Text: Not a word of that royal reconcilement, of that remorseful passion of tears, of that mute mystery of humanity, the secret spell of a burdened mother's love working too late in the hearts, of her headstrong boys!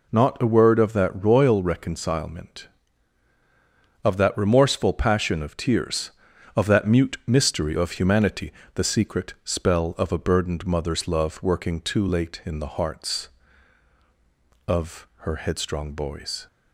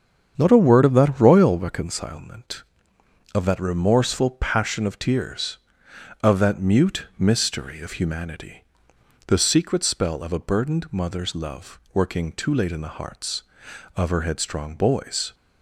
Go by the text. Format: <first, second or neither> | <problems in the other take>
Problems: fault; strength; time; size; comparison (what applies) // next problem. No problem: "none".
first | starts louder than the rest; strong; until 2.1 s; 7.5 dB // pauses between "love" and "working"; slight; at 11.7 s; 0.16 s long